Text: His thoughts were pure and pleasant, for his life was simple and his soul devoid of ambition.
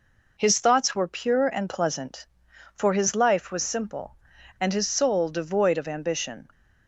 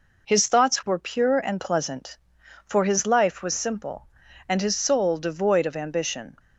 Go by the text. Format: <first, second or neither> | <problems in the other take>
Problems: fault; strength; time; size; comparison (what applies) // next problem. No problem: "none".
neither | none